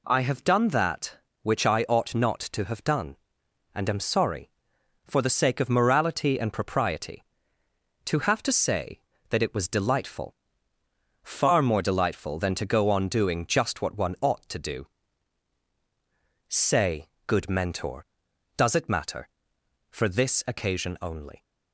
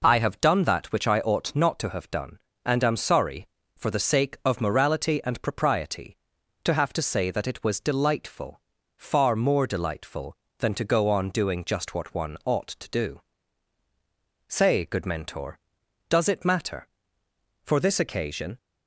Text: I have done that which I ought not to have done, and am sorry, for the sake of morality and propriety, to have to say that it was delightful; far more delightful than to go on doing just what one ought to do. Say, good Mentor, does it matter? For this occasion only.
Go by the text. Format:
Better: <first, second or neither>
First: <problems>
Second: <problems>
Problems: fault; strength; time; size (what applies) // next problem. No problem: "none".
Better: first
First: none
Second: stops before "only"; at 18.5 s